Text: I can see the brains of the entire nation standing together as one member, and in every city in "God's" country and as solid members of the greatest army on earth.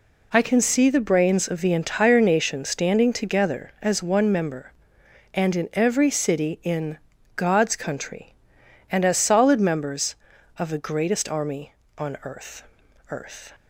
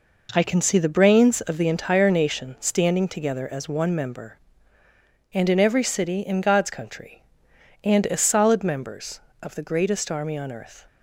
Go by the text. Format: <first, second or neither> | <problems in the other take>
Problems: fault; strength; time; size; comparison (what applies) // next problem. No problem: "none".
second | pauses between "in" and "God's"; at 6.9 s; 0.38 s long // says "earth" twice; at 13.0 s